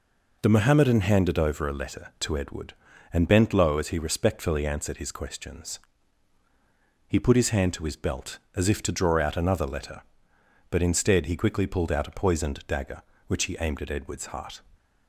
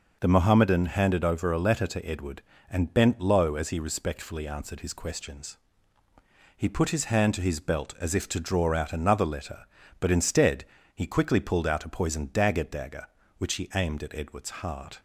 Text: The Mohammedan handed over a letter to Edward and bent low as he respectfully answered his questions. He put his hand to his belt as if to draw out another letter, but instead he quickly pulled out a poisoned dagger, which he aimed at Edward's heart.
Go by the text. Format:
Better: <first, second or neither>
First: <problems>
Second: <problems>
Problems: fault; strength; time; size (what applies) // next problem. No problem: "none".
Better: first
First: none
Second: pauses between "instead" and "he"; slight; at 10.6 s; 0.28 s long // says "dagger" twice; at 12.6 s